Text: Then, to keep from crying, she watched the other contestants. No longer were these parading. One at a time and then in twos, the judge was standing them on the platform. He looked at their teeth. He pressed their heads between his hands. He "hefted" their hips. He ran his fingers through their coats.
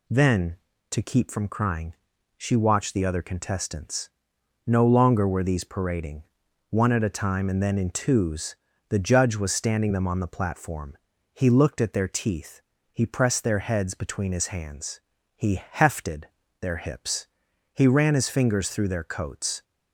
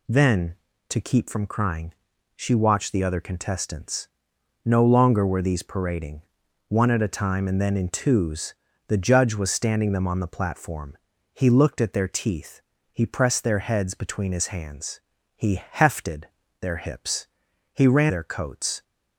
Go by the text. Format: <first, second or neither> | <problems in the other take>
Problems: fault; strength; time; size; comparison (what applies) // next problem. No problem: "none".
first | pauses between "hefted" and "their"; slight; at 16.2 s; 0.34 s long; slight in the first // skips "his fingers through"; at 18.0 s